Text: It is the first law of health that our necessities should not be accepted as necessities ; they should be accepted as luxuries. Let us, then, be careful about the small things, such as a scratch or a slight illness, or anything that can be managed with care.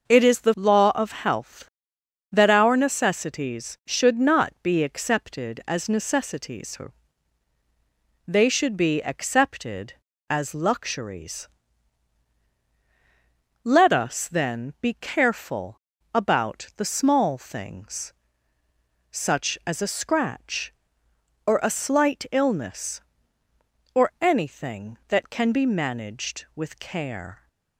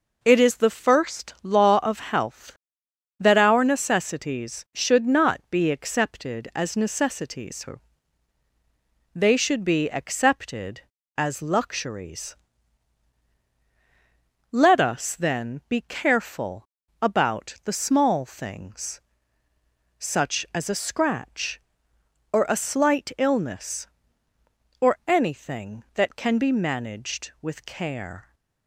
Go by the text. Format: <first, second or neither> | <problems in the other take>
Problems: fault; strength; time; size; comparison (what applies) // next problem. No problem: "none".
second | skips "first"; at 0.5 s // pauses between "careful" and "about"; slight; at 15.7 s; 0.34 s long; slight in the second